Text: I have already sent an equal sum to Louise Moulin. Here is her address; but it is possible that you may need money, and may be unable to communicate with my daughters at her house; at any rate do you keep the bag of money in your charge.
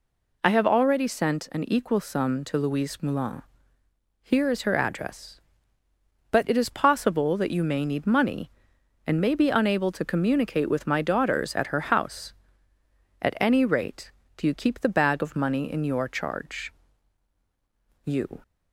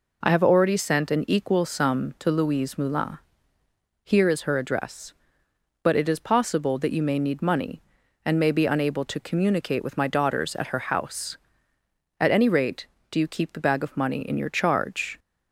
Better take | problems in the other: second | goes on to say "You"; slight; from 18.0 s on; 0.36 s long

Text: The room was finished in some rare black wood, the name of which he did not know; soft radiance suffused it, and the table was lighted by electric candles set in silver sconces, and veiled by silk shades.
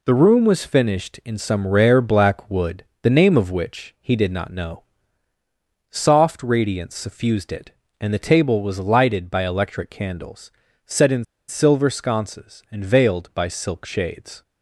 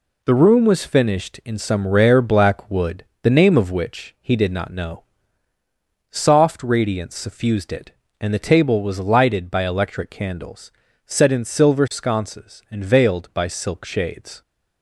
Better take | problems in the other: second | pauses between "candles" and "set"; slight; at 10.5 s; 0.36 s long; slight in the second // pauses between "in" and "silver"; slight; at 11.2 s; 0.24 s long

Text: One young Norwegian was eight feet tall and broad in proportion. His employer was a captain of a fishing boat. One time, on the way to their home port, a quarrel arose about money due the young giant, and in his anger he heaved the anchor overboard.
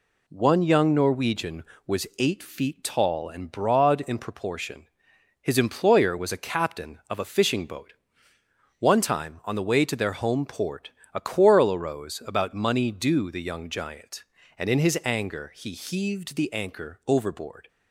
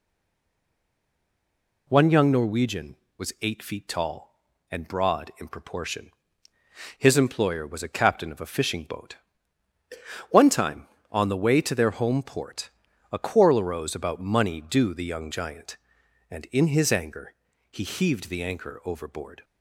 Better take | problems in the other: first | stays silent before the first word; noticeable; until 1.8 s; 1.8 s long // pauses between "anger" and "he"; slight; at 17.3 s; 0.36 s long

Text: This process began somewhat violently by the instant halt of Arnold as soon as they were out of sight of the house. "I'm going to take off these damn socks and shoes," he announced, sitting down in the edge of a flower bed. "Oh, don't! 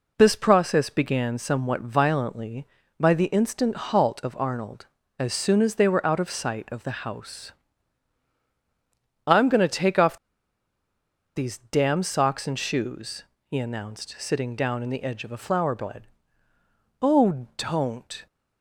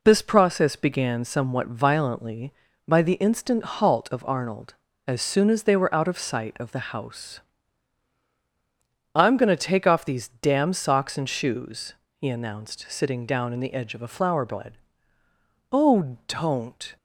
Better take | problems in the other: second | pauses between "off" and "these"; at 10.1 s; 1.1 s long

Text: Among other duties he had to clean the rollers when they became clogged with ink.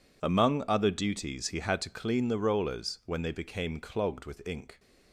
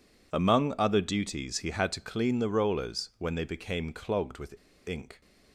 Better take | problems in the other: first | pauses between "with" and "ink"; slight; at 4.5 s; 0.34 s long

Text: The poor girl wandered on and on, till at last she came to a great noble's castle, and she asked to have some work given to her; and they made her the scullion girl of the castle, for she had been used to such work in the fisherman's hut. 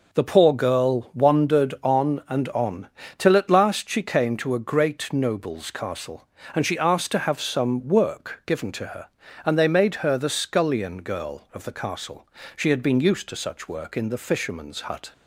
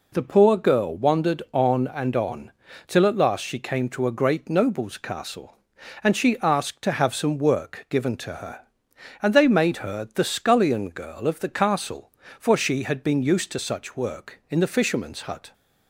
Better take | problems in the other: second | skips "for"; at 12.4 s

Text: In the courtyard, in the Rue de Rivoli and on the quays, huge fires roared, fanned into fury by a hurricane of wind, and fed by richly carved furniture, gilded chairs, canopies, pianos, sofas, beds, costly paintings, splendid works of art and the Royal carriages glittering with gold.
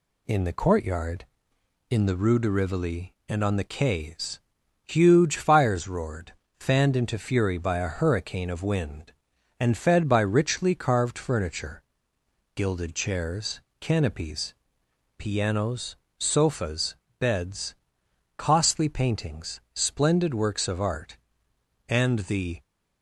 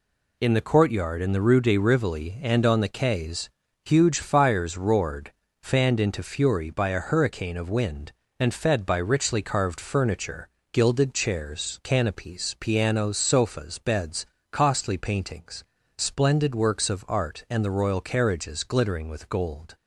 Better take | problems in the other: second | stops before "Royal carriages glittering with gold"; at 22.6 s

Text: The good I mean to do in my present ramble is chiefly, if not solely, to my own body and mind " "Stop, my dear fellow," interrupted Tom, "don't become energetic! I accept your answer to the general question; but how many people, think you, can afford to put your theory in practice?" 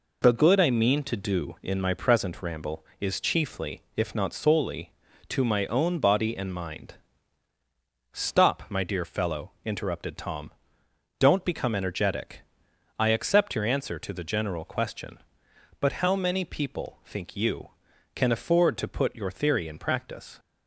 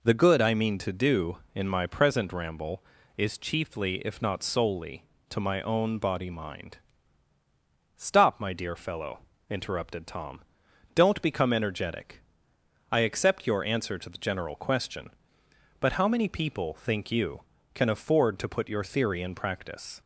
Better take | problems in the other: first | skips "and"; at 6.3 s

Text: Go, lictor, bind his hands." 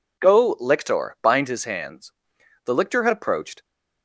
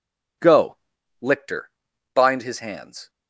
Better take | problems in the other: second | goes on to say "The lictor had approached"; noticeable; from 2.6 s on; 1.0 s long

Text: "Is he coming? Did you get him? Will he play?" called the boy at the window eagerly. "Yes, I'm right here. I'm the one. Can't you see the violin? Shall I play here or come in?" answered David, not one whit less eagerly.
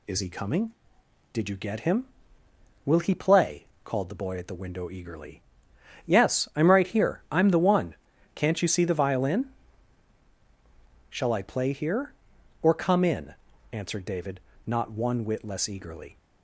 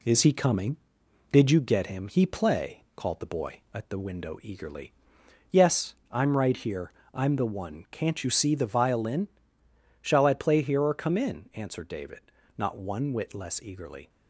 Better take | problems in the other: first | skips "Will"; at 2.0 s

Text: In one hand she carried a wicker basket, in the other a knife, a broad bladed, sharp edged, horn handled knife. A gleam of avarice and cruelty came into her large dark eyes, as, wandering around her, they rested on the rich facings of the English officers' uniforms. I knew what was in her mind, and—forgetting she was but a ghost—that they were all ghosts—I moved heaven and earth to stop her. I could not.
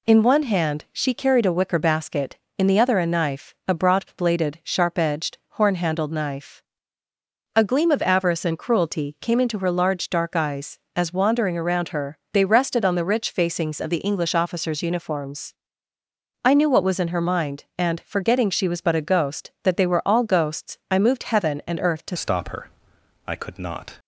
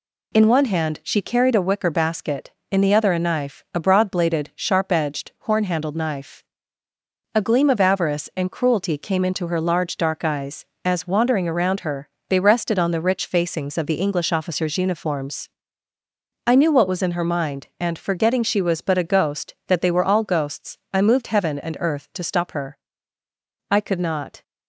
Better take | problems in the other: second | changes voice at "stop"; from 22.1 s on; 1.8 s long

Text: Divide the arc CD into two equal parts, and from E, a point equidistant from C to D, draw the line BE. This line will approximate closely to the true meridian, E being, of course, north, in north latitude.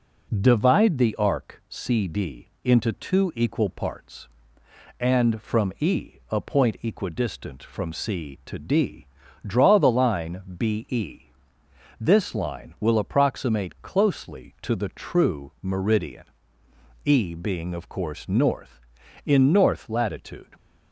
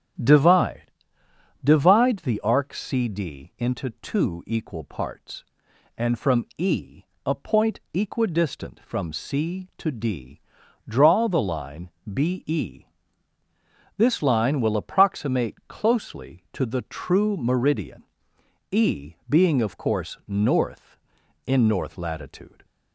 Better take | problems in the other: first | starts louder than the rest; strong; until 2.0 s; 10 dB // says "Divide" twice; at 1.6 s // pauses between "line" and "BE"; slight; at 11.8 s; 0.22 s long; slight in the first

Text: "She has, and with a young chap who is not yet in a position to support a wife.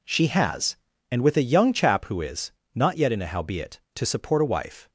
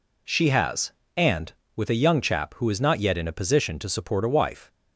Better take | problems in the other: second | pauses between "is" and "not"; slight; at 2.5 s; 0.22 s long // says "howbeit" for "position"; at 3.2 s

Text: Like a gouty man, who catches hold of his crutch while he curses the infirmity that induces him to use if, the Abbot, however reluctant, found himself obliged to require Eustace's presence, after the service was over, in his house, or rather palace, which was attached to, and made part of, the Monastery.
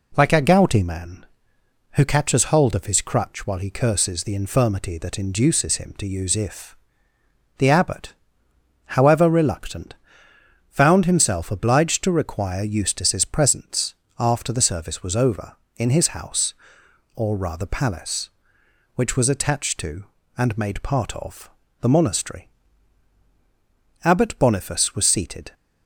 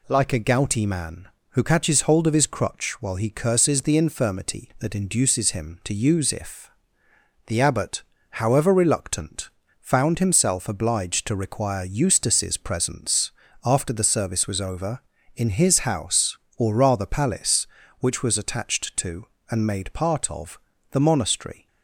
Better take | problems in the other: second | goes on to say "Abbot Boniface was seated"; from 24.0 s on; 1.5 s long

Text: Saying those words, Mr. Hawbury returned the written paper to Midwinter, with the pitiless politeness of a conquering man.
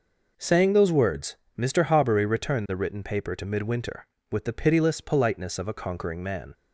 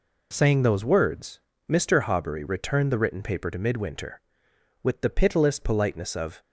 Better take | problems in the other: first | stops before "a conquering man"; at 6.4 s

